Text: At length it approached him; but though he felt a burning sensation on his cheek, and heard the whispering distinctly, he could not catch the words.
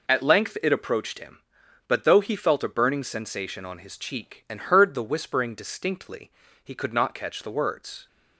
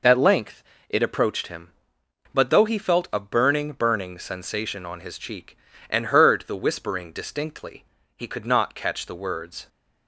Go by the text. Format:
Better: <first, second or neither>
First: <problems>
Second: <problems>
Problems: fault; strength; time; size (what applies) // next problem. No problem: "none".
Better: first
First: none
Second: pauses between "length" and "it"; slight; at 0.6 s; 0.28 s long // says "burning" twice; at 3.7 s